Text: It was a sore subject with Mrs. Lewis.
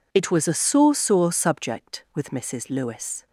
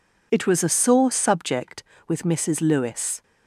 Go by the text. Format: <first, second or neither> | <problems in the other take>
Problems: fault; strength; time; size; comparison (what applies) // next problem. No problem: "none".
second | says "sore" twice; at 0.9 s